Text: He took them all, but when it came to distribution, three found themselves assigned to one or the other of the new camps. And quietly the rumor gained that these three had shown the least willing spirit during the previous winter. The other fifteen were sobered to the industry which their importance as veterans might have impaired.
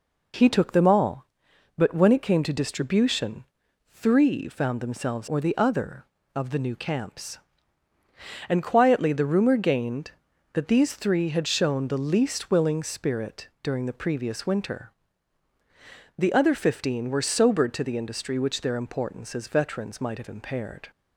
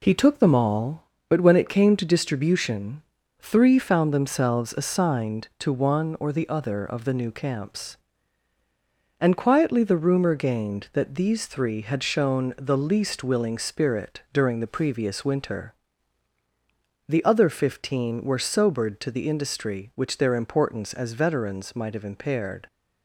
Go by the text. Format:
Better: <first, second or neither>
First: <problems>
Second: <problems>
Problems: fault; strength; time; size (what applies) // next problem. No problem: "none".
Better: second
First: skips "assigned to one"; at 5.2 s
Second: none